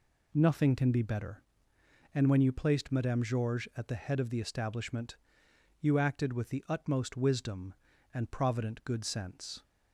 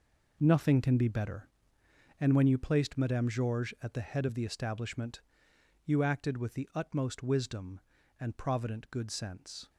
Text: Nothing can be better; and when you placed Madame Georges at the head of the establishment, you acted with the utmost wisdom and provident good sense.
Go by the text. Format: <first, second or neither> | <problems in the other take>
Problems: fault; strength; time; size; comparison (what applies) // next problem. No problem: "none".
first | gets quieter; strong; throughout; 11.5 dB